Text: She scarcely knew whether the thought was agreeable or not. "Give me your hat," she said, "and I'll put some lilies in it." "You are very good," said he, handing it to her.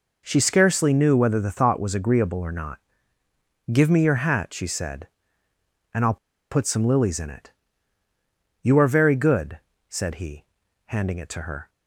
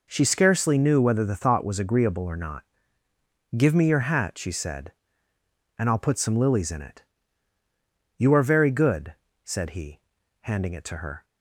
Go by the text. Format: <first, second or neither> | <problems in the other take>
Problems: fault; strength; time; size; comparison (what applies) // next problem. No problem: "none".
second | pauses between "I'll" and "put"; slight; at 6.1 s; 0.34 s long